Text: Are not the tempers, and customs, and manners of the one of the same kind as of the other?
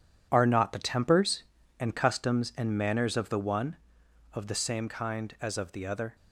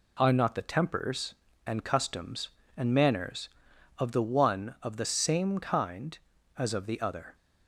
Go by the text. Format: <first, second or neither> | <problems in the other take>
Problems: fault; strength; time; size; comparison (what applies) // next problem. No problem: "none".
second | gets quieter; strong; throughout; 9.5 dB